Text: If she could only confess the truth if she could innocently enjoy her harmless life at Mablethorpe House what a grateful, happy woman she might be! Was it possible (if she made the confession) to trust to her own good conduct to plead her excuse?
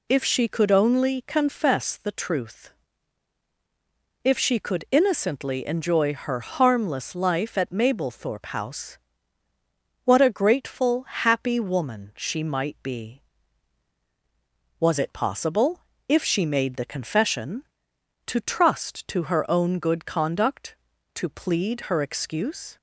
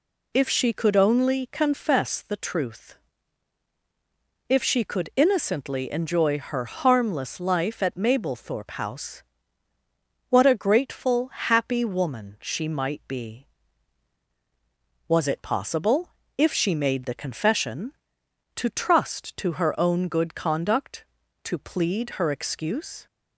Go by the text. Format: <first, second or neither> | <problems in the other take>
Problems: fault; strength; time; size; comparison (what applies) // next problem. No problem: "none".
neither | pauses between "truth" and "if"; strong; the same in both // pauses between "House" and "what"; the same in both